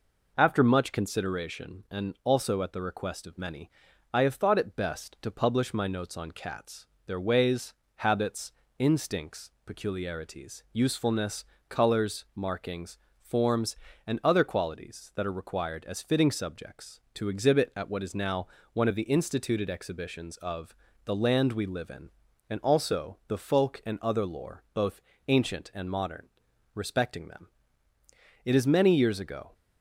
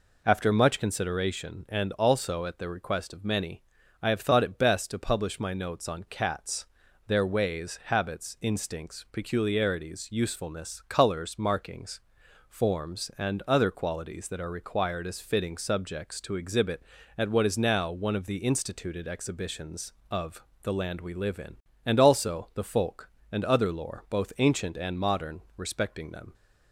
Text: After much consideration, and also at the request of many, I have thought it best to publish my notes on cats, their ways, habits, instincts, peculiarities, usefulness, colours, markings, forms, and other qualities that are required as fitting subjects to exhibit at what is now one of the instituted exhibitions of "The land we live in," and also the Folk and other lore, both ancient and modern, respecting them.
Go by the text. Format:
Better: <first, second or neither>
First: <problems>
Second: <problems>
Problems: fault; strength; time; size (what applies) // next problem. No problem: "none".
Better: second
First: pauses between "now" and "one"; slight; at 18.4 s; 0.24 s long // pauses between "of" and "The"; slight; at 20.7 s; 0.32 s long // pauses between "both" and "ancient"; slight; at 24.9 s; 0.28 s long // goes on to say "It is many years ago"; noticeable; from 28.4 s on; 1.1 s long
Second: pauses between "of" and "The"; slight; at 20.4 s; 0.18 s long